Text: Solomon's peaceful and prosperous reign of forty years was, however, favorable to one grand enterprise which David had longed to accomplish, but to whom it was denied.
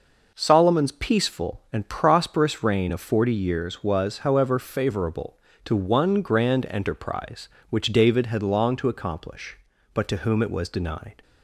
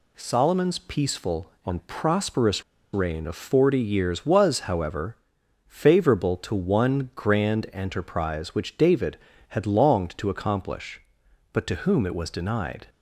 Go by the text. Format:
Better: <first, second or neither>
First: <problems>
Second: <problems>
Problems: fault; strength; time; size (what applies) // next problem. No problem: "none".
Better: first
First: none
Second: pauses between "prosperous" and "reign"; slight; at 2.6 s; 0.30 s long